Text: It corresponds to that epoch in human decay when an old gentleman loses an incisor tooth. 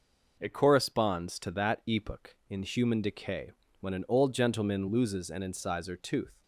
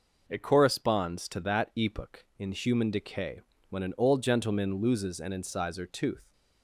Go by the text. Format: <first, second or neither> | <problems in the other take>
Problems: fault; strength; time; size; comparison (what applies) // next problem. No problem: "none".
neither | pauses between "decay" and "when"; slight; the same in both